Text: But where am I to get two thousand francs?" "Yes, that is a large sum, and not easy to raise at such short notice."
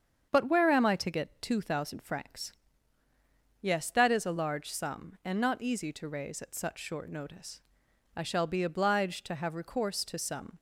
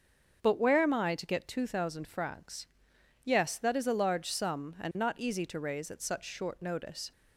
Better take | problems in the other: second | starts louder than the rest; strong; until 1.3 s; 7.5 dB; also in the second // goes on to say "I shall be obliged to have recourse to some"; strong; from 8.1 s on; 2.4 s long

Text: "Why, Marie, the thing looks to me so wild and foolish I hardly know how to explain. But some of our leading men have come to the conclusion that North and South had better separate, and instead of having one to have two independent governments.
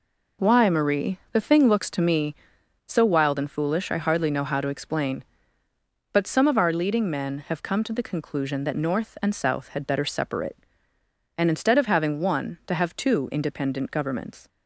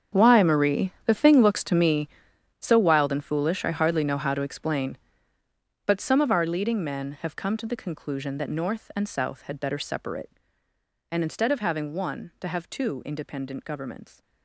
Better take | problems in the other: first | gets quieter; strong; throughout; 15.5 dB

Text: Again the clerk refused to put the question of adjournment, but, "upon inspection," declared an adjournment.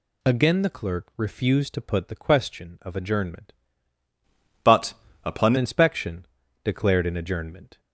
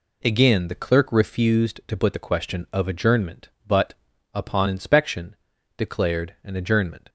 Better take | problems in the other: second | changes voice from "but" to "upon"; from 4.6 to 5.5 s; 0.9 s long

